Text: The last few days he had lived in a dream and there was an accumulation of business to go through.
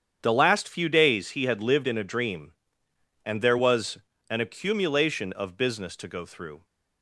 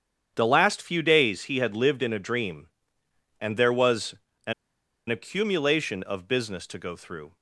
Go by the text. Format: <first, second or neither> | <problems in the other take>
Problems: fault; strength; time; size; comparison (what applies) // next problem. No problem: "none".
first | starts louder than the rest; strong; until 1.3 s; 8.5 dB; strong in the first // pauses between "was" and "an"; slight; at 4.1 s; 0.34 s long; slight in the first // pauses between "an" and "accumulation"; noticeable; at 4.5 s; 0.56 s long